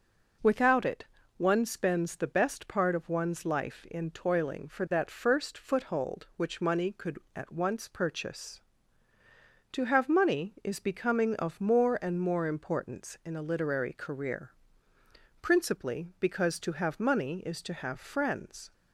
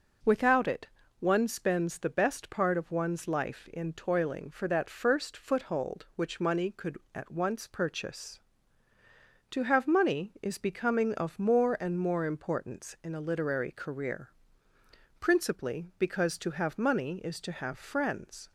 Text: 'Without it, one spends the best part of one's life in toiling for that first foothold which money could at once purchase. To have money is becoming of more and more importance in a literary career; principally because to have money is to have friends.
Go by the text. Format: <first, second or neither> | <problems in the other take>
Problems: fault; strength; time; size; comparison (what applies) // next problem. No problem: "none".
neither | none